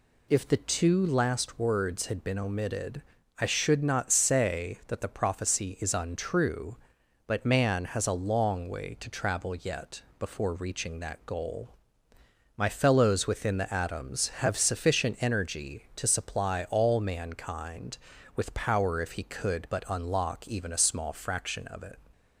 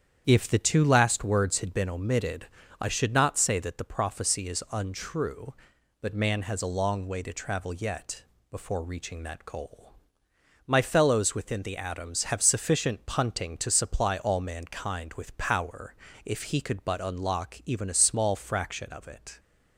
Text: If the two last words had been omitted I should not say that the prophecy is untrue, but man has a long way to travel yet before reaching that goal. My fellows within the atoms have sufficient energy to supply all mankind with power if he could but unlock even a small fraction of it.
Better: first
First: pauses between "omitted" and "I"; at 3.0 s; 0.38 s long // pauses between "yet" and "before"; slight; at 10.0 s; 0.18 s long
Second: starts louder than the rest; strong; until 1.2 s; 9 dB // pauses between "omitted" and "I"; slight; at 2.4 s; 0.34 s long // pauses between "yet" and "before"; slight; at 8.2 s; 0.28 s long // says "punting" for "energy"; at 13.0 s // pauses between "power" and "if"; slight; at 15.9 s; 0.32 s long

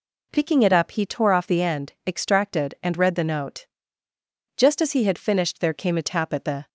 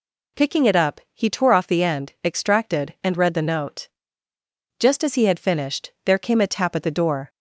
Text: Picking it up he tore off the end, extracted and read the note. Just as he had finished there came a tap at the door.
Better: second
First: stops before "door"; at 6.6 s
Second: none

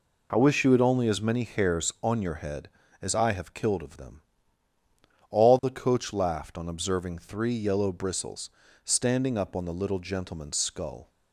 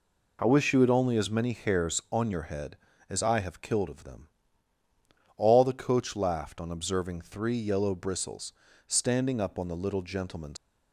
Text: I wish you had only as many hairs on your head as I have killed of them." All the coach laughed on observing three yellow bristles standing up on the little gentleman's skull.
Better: first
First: pauses between "bristles" and "standing"; slight; at 8.4 s; 0.34 s long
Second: pauses between "bristles" and "standing"; slight; at 8.5 s; 0.34 s long // stops before "skull"; at 10.5 s

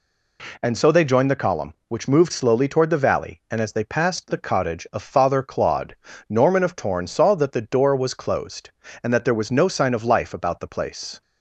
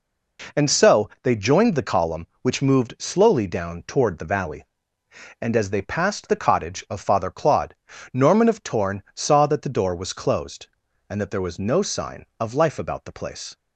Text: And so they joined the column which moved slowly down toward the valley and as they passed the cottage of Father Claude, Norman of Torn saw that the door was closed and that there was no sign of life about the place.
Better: second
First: skips "down"; at 2.6 s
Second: none

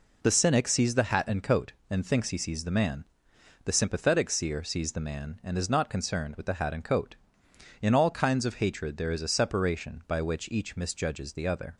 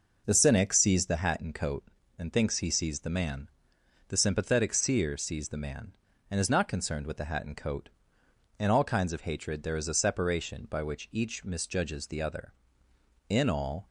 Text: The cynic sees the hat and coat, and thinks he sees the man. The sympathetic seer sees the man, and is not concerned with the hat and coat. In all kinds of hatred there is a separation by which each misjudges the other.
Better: first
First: none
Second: goes on to say "In all"; from 13.2 s on; 0.58 s long

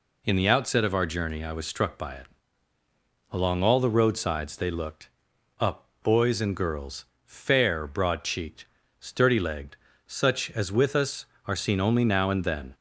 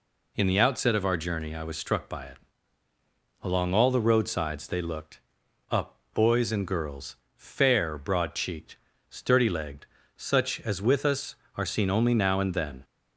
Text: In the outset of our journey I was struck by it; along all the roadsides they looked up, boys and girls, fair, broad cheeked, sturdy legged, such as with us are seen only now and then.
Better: neither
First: pauses between "looked" and "up"; noticeable; at 5.0 s; 0.54 s long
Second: pauses between "looked" and "up"; noticeable; at 5.1 s; 0.54 s long

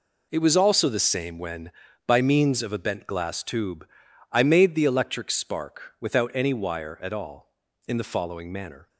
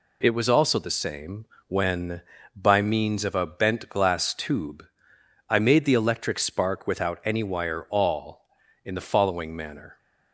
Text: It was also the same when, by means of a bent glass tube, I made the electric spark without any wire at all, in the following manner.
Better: first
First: none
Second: pauses between "same" and "when"; slight; at 1.4 s; 0.22 s long // skips "at"; at 7.8 s

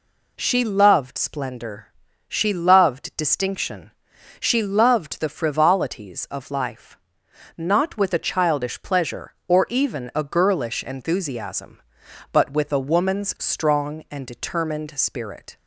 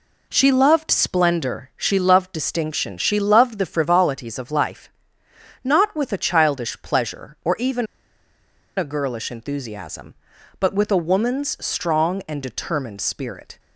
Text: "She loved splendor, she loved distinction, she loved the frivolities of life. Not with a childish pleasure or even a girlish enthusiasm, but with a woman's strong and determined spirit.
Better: first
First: none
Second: pauses between "even" and "a"; noticeable; at 7.8 s; 0.92 s long

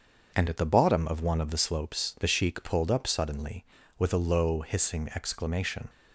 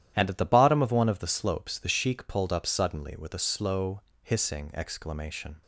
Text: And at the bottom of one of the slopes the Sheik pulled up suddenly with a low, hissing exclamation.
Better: first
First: starts louder than the rest; until 1.3 s; 6.5 dB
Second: starts louder than the rest; strong; until 1.1 s; 11.5 dB // says "slow" for "low"; at 3.4 s

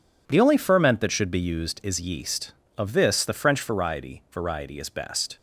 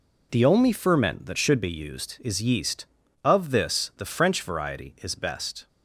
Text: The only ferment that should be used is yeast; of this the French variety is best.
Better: second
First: says "variety" twice; at 4.3 s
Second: none

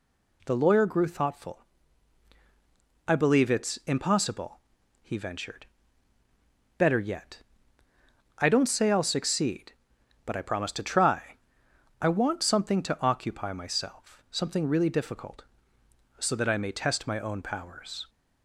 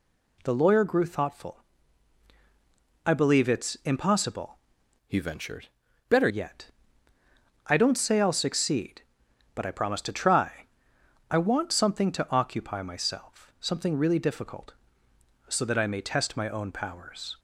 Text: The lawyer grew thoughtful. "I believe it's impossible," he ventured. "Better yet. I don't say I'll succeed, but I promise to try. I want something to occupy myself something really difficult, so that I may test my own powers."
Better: first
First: pauses between "myself" and "something"; slight; at 14.1 s; 0.16 s long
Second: changes voice from "he" to "Better"; from 5.0 to 6.2 s; 1.2 s long // pauses between "myself" and "something"; slight; at 13.4 s; 0.16 s long

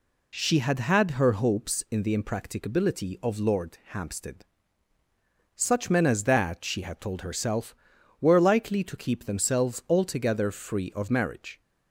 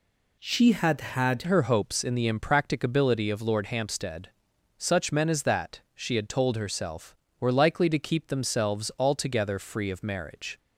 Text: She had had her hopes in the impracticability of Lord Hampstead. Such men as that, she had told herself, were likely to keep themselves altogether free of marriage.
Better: first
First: none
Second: changes voice at "her"; from 1.4 s on; 9.1 s long

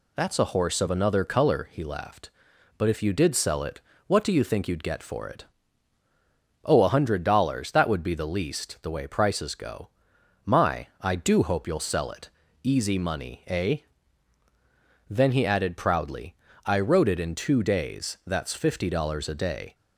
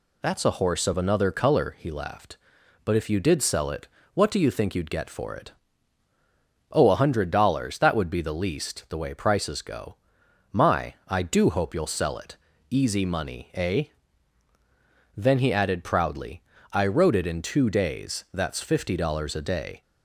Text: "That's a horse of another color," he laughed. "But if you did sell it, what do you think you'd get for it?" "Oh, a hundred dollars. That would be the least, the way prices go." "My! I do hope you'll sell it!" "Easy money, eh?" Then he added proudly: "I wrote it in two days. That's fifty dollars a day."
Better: neither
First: none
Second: none

